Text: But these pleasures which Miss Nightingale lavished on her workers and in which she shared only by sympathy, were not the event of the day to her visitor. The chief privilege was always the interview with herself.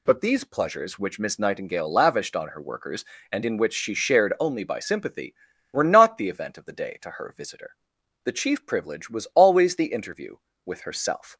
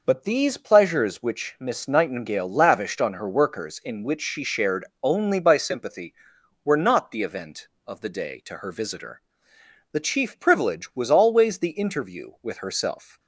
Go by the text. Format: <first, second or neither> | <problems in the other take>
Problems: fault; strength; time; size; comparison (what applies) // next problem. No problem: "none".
first | skips "and"; at 3.8 s // pauses between "shared" and "only"; slight; at 4.8 s; 0.16 s long